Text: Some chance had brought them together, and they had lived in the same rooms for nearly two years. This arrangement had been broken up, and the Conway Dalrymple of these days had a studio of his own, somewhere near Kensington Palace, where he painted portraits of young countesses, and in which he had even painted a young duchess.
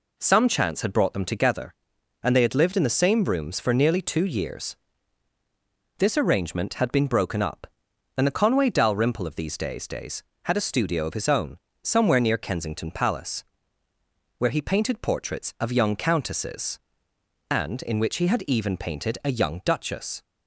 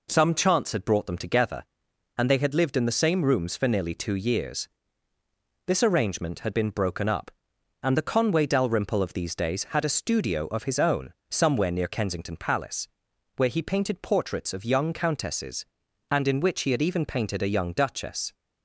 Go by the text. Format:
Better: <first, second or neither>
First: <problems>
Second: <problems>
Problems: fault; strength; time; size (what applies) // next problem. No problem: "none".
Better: second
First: says "days" twice; at 9.8 s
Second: none